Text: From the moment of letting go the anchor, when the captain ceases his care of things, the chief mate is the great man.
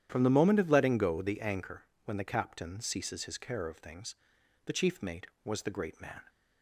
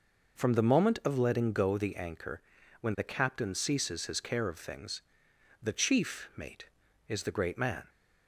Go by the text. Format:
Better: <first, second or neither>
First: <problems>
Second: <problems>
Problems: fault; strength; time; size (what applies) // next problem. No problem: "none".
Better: second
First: starts louder than the rest; strong; until 1.1 s; 10.5 dB // says "was" for "is"; at 5.4 s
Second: none